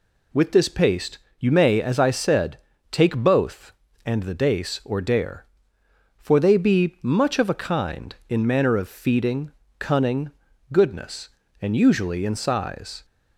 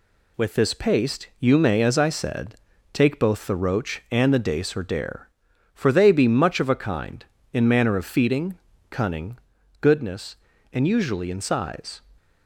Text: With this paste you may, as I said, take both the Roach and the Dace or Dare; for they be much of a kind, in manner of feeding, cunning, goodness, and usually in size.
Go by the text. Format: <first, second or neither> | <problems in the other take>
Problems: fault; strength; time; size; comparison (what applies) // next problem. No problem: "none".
second | pauses between "paste" and "you"; slight; at 1.1 s; 0.22 s long // skips "the Roach"; at 3.8 s